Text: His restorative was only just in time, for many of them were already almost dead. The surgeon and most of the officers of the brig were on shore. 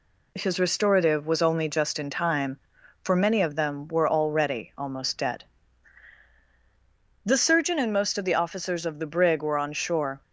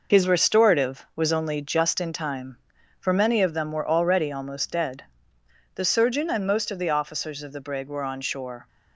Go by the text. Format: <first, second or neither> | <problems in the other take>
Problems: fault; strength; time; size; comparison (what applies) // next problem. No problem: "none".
first | gets quieter; noticeable; throughout; 6 dB